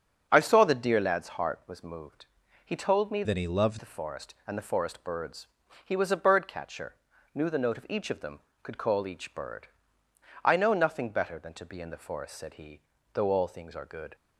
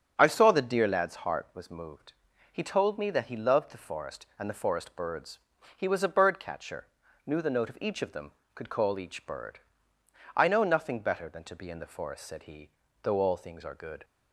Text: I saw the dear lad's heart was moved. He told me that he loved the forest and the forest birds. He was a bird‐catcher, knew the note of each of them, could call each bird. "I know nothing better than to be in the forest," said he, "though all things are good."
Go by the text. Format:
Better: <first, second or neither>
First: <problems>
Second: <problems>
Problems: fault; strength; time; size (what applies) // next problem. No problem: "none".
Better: second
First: starts louder than the rest; until 1.3 s; 7 dB // changes voice from "that" to "loved"; from 3.2 to 3.7 s; 0.5 s long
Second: starts louder than the rest; strong; until 1.1 s; 7 dB